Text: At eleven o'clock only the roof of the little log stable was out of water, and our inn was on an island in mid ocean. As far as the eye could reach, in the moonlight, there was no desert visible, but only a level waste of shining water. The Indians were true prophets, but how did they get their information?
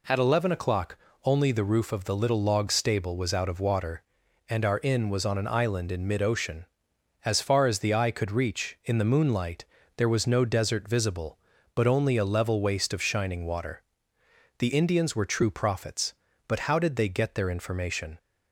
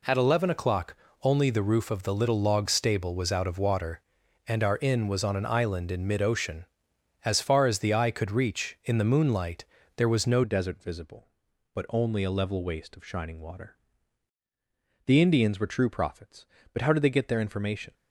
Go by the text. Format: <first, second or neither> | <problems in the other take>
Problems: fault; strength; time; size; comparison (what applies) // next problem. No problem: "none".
first | pauses between "o'clock" and "only"; slight; at 0.9 s; 0.26 s long; slight in the first // changes voice at "desert"; from 10.4 s on; 7.5 s long